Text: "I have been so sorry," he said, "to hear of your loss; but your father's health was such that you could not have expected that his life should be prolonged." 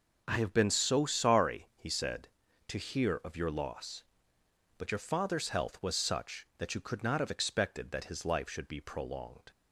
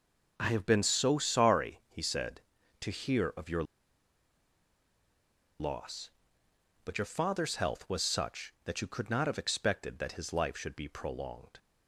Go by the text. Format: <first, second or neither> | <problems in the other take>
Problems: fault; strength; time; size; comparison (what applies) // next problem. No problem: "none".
first | pauses between "your" and "loss"; strong; at 3.6 s; 1.9 s long